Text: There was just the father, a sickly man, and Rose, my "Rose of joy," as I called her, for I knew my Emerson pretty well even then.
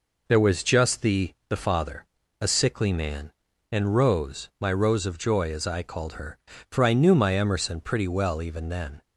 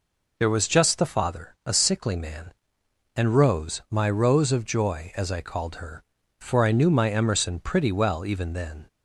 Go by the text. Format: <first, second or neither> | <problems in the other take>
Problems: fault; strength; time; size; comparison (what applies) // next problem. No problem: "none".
second | says "the" twice; at 1.4 s